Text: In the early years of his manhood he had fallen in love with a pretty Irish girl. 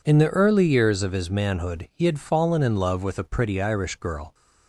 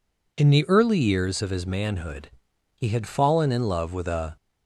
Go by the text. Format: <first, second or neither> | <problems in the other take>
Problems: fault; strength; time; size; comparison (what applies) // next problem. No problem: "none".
first | pauses between "manhood" and "he"; noticeable; at 2.2 s; 0.46 s long // stops before "pretty Irish girl"; at 4.3 s